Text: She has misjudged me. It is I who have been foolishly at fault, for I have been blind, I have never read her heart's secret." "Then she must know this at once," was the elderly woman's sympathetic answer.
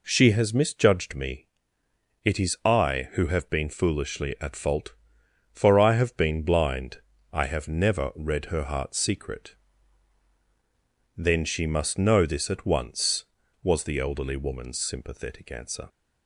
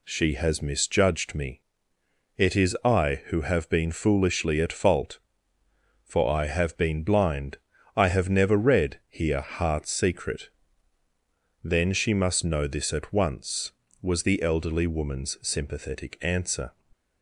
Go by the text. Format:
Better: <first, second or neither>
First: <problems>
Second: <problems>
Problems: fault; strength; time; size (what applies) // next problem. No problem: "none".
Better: first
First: none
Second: says "here" for "her"; at 9.0 s